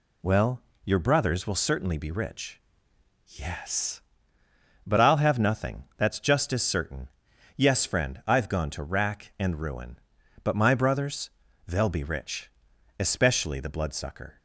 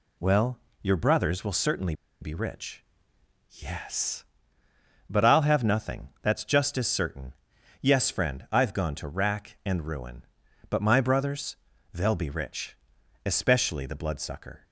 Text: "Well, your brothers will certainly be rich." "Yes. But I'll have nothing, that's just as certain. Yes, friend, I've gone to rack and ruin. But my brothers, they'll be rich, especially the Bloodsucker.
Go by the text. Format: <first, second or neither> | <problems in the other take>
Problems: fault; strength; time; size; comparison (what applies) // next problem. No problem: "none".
first | pauses between "certainly" and "be"; slight; at 1.9 s; 0.27 s long